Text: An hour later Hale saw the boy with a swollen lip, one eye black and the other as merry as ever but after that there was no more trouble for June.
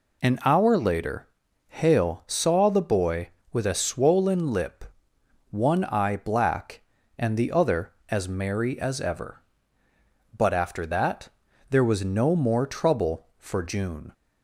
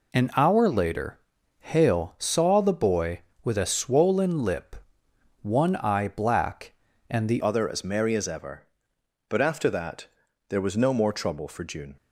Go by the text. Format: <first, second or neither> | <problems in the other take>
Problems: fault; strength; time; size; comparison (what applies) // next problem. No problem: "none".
first | pauses between "later" and "Hale"; at 1.1 s; 0.40 s long; also in the first // changes voice at "other"; from 7.4 s on; 4.5 s long // pauses between "that" and "there"; at 10.0 s; 0.42 s long; also in the first